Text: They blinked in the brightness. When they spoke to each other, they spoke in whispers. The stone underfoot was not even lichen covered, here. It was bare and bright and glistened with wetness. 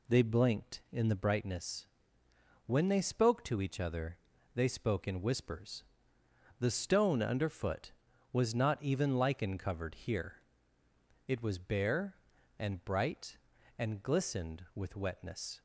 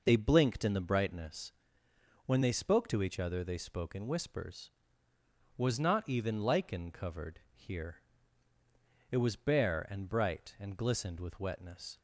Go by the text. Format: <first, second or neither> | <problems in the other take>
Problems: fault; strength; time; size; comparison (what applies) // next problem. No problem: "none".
first | skips "The stone underfoot"; at 5.1 s